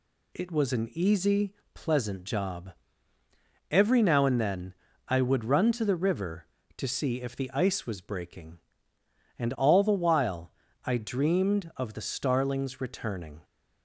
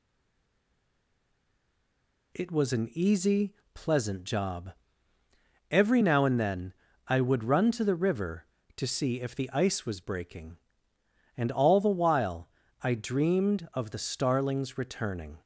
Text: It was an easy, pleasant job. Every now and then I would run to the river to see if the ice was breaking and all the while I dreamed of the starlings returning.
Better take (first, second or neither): first